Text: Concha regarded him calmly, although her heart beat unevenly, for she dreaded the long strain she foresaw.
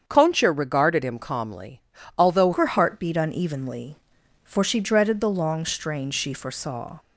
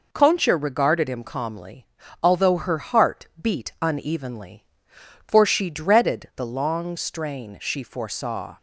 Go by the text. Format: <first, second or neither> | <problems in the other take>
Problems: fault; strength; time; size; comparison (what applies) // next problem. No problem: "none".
second | starts louder than the rest; strong; until 1.0 s; 7.5 dB // changes voice at "her"; from 2.5 s on; 4.4 s long